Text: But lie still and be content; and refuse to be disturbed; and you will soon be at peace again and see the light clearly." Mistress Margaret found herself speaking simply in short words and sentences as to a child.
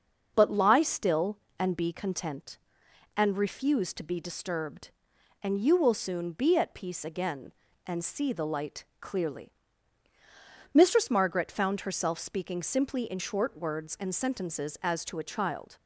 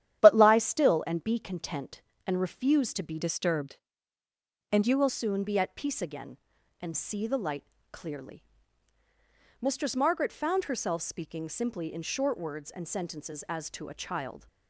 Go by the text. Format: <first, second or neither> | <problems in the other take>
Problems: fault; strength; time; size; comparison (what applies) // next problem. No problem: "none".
first | starts louder than the rest; strong; until 1.2 s; 11 dB; noticeable in the first // changes voice from "disturbed" to "will"; from 3.2 to 5.0 s; 1.8 s long // pauses between "light" and "clearly"; slight; at 7.6 s; 0.30 s long; slight in the first